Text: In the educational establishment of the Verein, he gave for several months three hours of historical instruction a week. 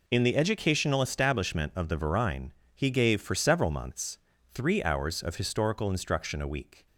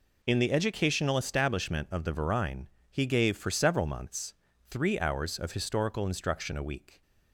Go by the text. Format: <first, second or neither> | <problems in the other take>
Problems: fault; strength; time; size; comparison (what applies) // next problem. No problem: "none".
neither | pauses between "months" and "three"; slight; the same in both